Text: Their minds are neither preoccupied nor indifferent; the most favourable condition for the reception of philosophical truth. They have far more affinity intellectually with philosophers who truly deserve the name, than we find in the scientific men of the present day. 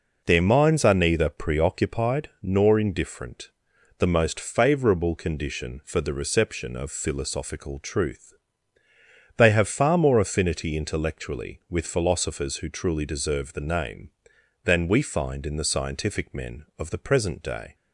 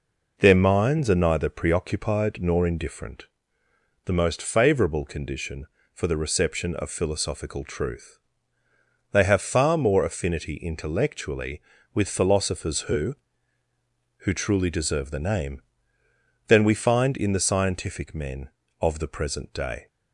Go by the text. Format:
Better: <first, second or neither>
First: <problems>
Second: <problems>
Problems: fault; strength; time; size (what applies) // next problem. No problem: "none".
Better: first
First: none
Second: says "who" twice; at 14.1 s